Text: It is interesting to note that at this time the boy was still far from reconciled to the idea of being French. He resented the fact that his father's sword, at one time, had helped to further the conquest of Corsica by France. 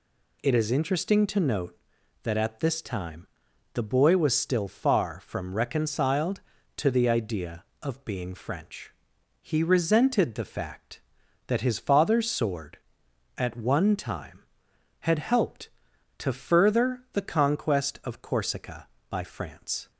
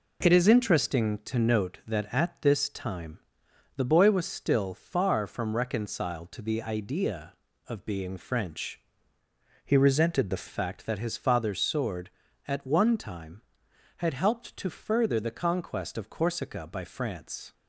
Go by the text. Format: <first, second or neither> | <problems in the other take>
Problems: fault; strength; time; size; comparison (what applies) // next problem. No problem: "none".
first | pauses between "time" and "the"; noticeable; at 3.1 s; 0.58 s long; noticeable in the first // changes voice from "He" to "the"; from 9.6 to 10.4 s; 0.8 s long